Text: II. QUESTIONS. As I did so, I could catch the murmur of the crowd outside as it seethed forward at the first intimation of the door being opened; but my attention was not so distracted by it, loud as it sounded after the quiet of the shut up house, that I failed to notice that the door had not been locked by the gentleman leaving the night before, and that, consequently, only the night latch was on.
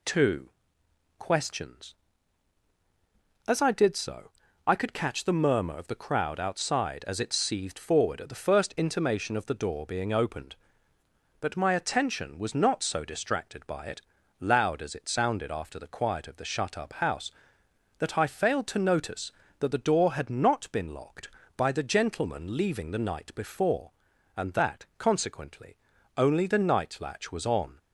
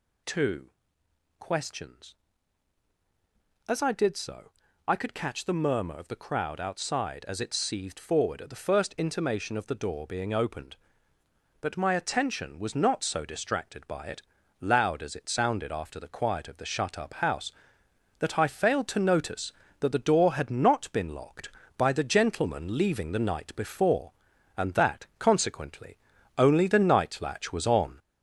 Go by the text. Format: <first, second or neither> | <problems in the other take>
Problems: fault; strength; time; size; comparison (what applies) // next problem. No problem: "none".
first | gets louder; noticeable; throughout; 4.5 dB